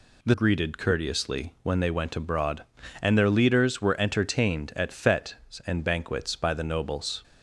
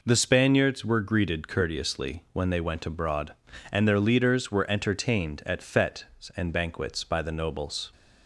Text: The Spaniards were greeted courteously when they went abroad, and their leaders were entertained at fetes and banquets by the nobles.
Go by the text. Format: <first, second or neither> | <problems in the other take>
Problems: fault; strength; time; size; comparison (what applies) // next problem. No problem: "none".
second | skips "Spaniards were"; at 0.3 s